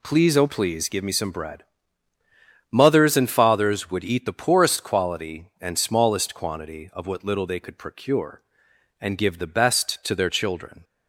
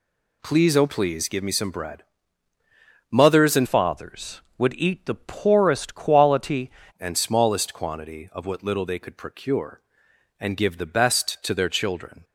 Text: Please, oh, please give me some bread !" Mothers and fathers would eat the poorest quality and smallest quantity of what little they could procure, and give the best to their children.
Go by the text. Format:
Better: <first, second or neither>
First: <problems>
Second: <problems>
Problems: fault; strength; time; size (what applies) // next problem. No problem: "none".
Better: first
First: none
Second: changes voice from "fathers" to "quality"; from 3.6 to 6.7 s; 3.1 s long